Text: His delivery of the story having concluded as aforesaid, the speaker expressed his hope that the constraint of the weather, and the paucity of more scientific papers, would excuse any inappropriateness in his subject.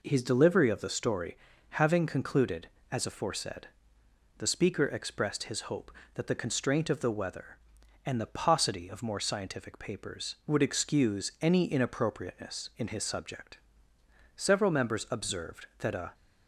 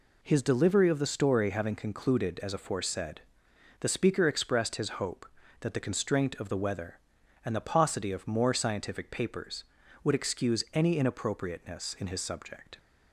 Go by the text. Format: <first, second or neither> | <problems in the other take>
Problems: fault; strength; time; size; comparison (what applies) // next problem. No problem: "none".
second | pauses between "story" and "having"; at 1.3 s; 0.38 s long // goes on to say "Several members observed that a"; strong; from 14.3 s on; 1.7 s long